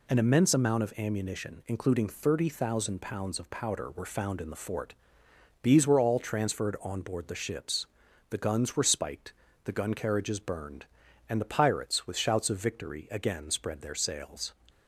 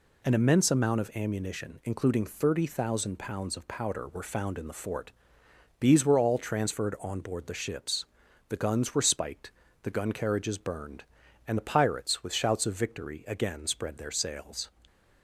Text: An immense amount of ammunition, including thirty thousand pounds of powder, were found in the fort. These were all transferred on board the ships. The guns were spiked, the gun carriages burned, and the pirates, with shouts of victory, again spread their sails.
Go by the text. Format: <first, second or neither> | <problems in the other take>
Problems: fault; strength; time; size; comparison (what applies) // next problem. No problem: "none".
neither | none